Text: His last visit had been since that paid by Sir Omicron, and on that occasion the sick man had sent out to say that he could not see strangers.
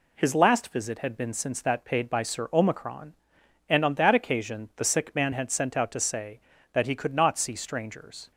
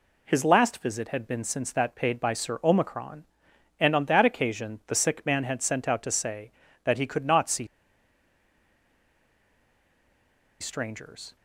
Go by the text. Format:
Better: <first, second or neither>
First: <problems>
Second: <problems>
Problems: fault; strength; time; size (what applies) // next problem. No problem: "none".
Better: first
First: none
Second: pauses between "see" and "strangers"; strong; at 7.6 s; 2.9 s long